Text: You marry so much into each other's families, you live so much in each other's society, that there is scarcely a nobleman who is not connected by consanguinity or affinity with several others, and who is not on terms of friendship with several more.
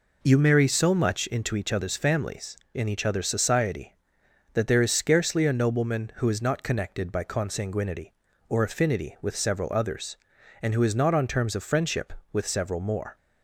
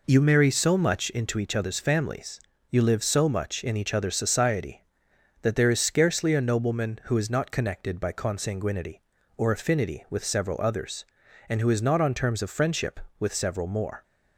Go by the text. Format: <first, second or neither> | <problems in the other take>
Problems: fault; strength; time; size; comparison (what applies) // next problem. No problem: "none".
second | skips "you live so much"; at 2.6 s